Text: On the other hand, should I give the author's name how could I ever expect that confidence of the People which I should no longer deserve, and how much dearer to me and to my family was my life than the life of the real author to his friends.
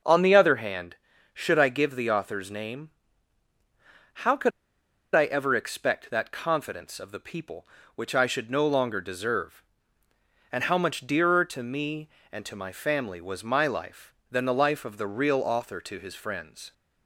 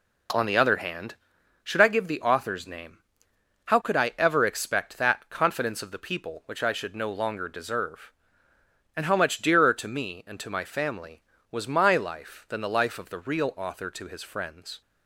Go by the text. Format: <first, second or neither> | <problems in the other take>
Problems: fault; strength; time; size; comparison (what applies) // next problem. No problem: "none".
second | starts louder than the rest; noticeable; until 1.4 s; 6 dB // pauses between "name" and "how"; strong; at 2.9 s; 1.2 s long; noticeable in the second // pauses between "could" and "I"; noticeable; at 4.5 s; 0.64 s long